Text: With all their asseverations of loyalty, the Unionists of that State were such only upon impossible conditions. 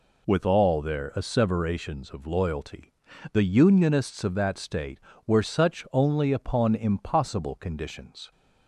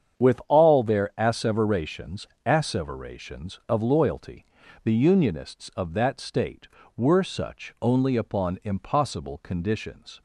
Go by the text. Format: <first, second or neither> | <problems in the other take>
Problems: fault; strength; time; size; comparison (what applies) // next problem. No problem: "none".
first | starts louder than the rest; strong; until 1.3 s; 8 dB // says "asseverations" twice; at 2.4 s